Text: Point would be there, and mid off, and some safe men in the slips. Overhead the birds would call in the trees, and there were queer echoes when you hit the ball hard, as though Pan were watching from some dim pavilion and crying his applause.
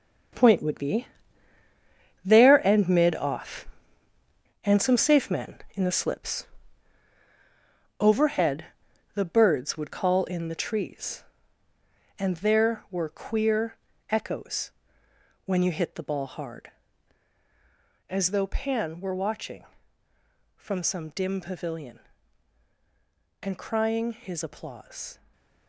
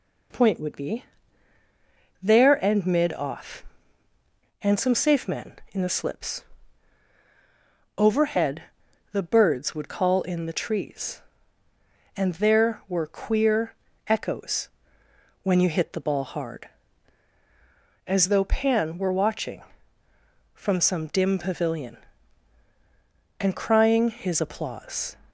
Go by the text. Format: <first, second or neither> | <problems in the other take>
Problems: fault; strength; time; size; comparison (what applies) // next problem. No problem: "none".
second | gets quieter; strong; throughout; 10 dB // pauses between "be" and "there"; at 1.0 s; 1.1 s long; also in the second // pauses between "Overhead" and "the"; noticeable; at 8.6 s; 0.48 s long; noticeable in the second // pauses between "queer" and "echoes"; slight; at 13.7 s; 0.34 s long; slight in the second // pauses between "echoes" and "when"; noticeable; at 14.7 s; 0.74 s long; noticeable in the second // stays silent after the last word; slight; from 25.1 s on; 0.5 s long